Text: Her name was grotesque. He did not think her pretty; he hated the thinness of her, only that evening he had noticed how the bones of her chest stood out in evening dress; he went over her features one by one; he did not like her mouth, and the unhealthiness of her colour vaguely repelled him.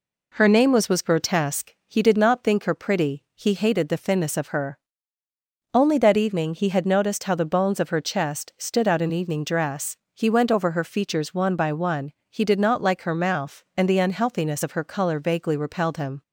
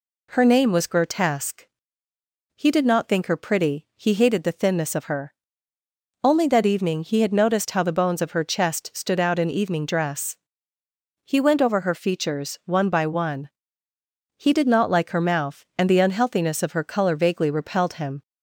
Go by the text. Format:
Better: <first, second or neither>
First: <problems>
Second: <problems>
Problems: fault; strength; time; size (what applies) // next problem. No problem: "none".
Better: second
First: says "was" twice; at 0.8 s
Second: none